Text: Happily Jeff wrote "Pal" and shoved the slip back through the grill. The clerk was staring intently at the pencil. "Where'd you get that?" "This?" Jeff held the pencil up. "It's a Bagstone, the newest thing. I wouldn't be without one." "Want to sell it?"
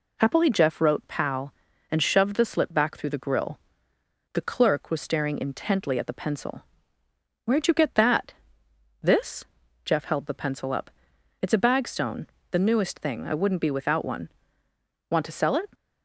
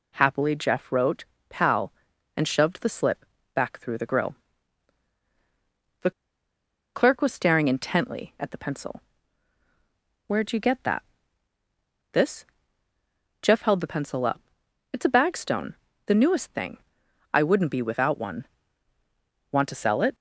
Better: first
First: none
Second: pauses between "wrote" and "Pal"; slight; at 1.2 s; 0.24 s long // pauses between "slip" and "back"; slight; at 3.2 s; 0.30 s long // pauses between "The" and "clerk"; noticeable; at 6.1 s; 0.84 s long

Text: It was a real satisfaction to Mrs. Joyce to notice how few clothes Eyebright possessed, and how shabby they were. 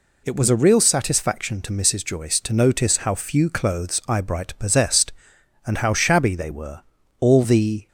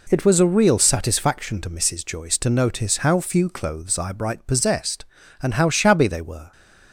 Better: second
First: goes on to say "All the"; noticeable; from 7.2 s on; 0.66 s long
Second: none

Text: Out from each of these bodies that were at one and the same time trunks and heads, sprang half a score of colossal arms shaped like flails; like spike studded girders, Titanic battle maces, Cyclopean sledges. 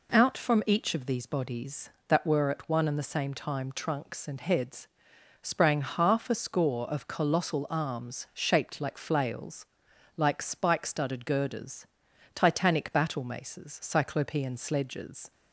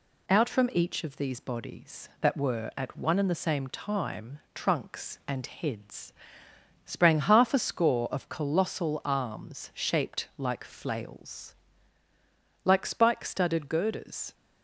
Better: first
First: none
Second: stops before "Titanic battle maces Cyclopean sledges"; at 14.3 s

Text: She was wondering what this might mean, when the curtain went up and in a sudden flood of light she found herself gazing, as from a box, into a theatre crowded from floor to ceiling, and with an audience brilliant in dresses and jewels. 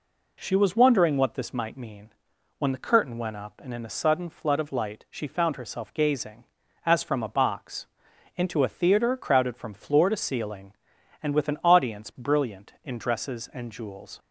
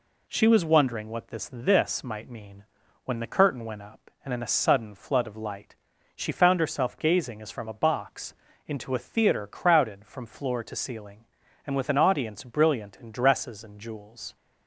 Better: first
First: none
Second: says "this" twice; at 1.5 s // pauses between "light" and "she"; at 5.7 s; 0.40 s long

